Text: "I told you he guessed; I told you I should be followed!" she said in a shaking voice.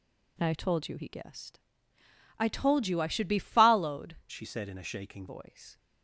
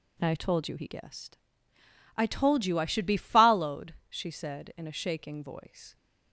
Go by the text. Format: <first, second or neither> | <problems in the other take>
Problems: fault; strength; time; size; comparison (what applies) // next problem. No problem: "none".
second | changes voice from "she" to "shaking"; from 4.3 to 5.2 s; 0.9 s long